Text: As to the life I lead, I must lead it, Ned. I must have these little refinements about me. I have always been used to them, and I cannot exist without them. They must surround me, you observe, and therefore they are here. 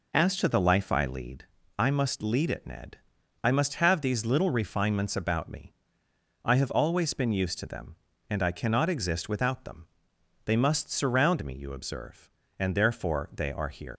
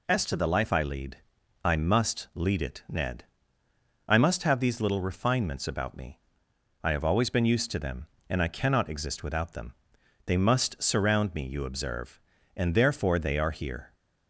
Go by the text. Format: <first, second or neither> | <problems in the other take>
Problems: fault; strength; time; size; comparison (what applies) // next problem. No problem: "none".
second | leaves "here" unfinished; at 13.9 s; 120 ms